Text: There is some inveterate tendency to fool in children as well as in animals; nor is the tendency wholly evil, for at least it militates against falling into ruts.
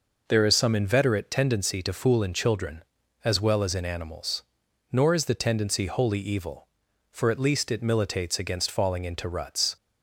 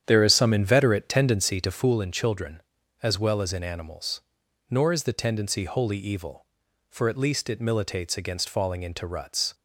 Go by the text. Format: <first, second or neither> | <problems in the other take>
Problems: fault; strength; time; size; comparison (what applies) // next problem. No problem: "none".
first | starts louder than the rest; strong; until 1.9 s; 9 dB